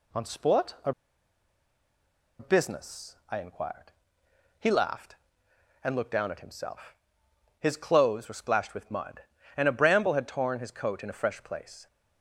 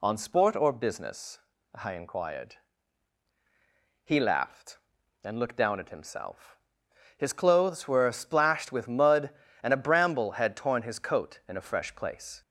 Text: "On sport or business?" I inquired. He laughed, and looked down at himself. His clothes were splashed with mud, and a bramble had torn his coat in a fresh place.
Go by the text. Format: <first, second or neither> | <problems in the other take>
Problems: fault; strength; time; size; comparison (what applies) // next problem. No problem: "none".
second | pauses between "or" and "business"; strong; at 0.9 s; 1.4 s long